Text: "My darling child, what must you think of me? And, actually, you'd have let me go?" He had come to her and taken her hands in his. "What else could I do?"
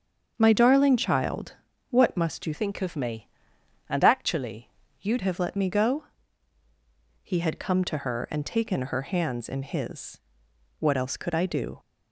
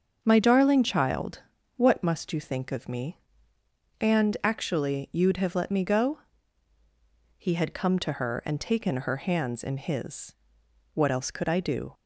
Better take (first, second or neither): second